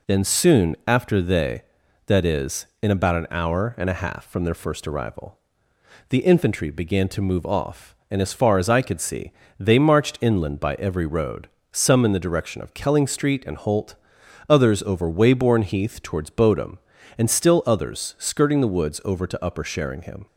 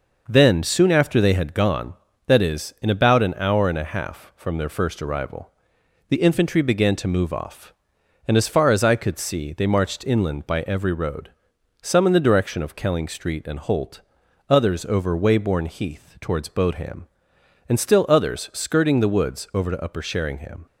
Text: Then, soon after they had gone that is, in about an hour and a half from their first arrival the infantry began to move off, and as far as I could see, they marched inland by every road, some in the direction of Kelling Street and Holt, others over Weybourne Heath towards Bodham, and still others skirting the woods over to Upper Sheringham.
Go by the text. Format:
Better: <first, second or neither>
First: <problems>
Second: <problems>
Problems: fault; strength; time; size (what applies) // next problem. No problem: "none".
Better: second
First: skips "had gone"; at 1.8 s // pauses between "arrival" and "the"; noticeable; at 5.3 s; 0.70 s long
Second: pauses between "arrival" and "the"; noticeable; at 5.5 s; 0.56 s long